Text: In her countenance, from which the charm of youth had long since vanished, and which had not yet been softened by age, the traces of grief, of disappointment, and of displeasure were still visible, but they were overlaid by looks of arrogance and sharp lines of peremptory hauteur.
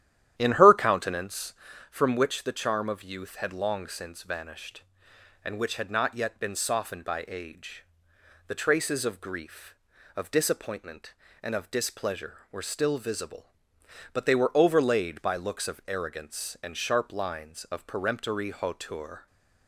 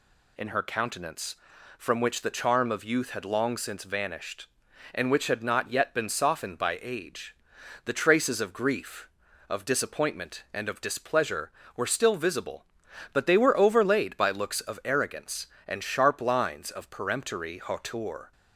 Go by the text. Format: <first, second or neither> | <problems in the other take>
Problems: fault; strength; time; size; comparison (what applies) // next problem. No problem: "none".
second | starts louder than the rest; strong; until 1.7 s; 11.5 dB